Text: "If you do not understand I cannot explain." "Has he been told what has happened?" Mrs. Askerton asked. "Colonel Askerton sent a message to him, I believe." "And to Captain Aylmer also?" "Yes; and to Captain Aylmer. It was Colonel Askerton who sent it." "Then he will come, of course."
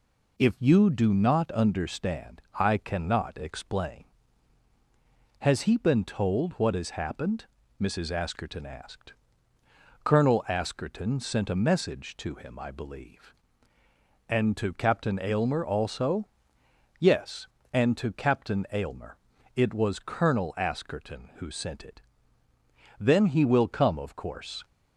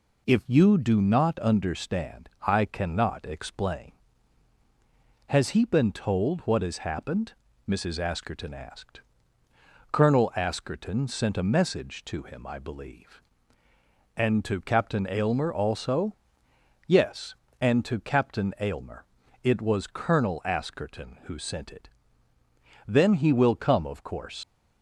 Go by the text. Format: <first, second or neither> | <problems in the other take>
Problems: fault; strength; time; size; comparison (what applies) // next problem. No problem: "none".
first | pauses between "understand" and "I"; slight; at 2.3 s; 0.16 s long; slight in the first // leaves "course" unfinished; at 24.4 s; 90 ms